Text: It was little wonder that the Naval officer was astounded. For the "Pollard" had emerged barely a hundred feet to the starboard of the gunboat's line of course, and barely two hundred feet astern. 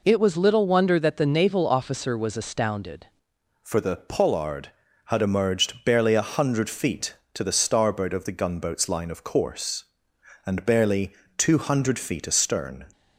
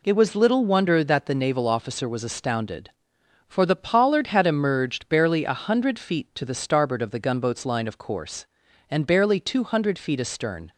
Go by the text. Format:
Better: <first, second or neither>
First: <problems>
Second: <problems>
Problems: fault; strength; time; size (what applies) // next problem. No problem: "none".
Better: second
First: changes voice at "For"; from 3.6 s on; 9.2 s long // pauses between "barely" and "two"; slight; at 11.1 s; 0.24 s long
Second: none